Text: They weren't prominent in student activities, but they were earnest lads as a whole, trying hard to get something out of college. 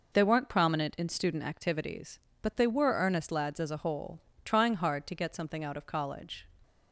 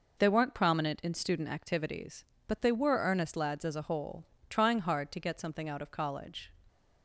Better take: neither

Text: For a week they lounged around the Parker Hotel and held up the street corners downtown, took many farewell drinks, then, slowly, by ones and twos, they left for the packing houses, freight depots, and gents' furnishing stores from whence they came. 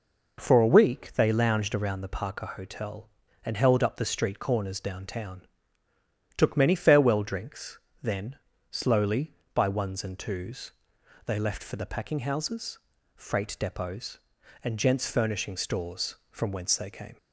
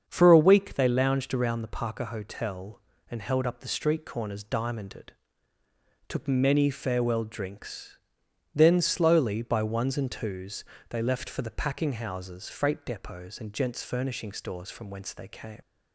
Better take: first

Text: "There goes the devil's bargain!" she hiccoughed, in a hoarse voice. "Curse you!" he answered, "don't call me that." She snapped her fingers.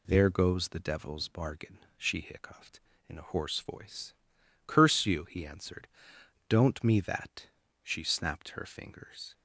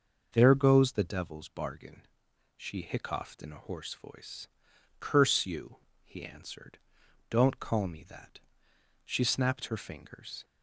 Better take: second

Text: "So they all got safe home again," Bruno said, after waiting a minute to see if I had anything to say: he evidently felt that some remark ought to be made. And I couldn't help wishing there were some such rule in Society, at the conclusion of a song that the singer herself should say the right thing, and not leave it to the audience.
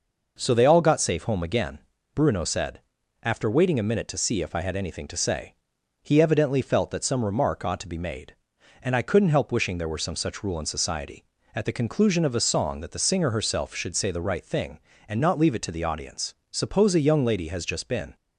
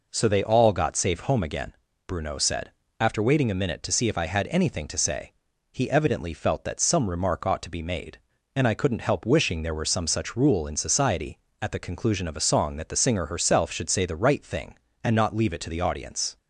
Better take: second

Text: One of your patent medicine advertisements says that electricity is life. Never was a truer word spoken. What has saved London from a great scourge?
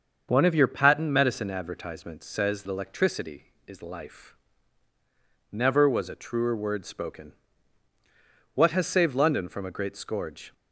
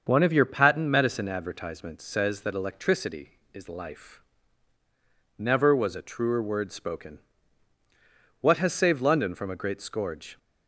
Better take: second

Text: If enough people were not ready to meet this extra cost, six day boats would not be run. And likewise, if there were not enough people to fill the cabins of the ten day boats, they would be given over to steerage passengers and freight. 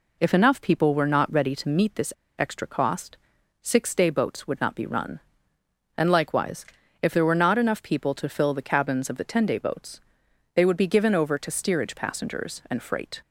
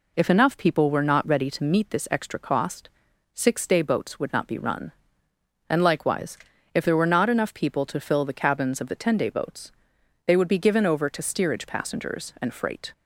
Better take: second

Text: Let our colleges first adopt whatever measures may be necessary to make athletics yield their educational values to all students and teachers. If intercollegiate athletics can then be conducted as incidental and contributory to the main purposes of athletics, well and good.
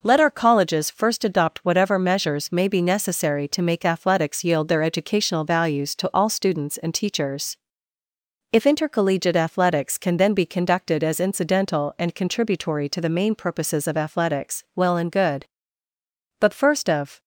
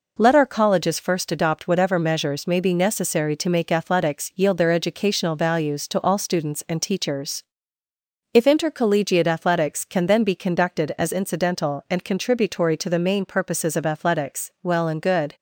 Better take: second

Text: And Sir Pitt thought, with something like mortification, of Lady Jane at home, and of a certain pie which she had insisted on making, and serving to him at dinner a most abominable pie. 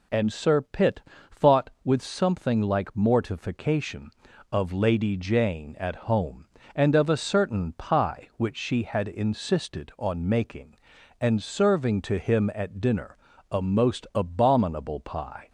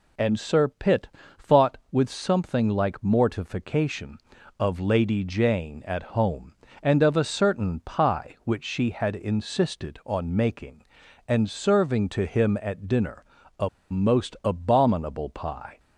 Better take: first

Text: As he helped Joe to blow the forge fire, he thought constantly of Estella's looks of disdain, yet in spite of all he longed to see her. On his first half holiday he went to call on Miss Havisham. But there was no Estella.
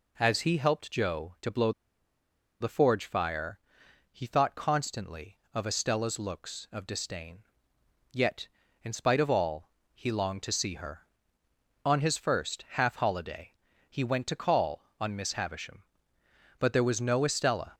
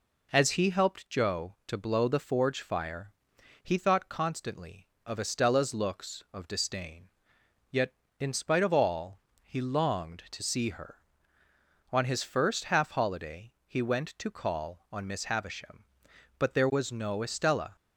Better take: second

